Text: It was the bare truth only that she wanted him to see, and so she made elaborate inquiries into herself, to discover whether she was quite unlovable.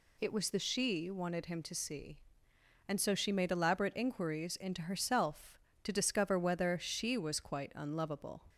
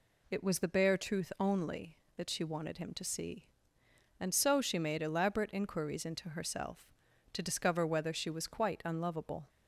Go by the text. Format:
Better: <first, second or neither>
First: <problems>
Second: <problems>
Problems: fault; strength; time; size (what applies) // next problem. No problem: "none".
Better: second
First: skips "bare truth only that"; at 0.5 s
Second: none